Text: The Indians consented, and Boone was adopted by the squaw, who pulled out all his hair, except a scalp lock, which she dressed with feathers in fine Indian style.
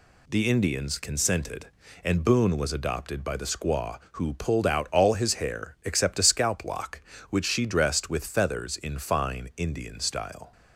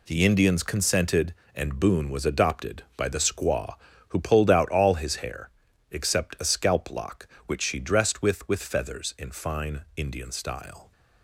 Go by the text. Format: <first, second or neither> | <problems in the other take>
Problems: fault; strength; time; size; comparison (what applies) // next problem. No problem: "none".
first | says "with" twice; at 8.4 s // pauses between "fine" and "Indian"; slight; at 9.8 s; 0.16 s long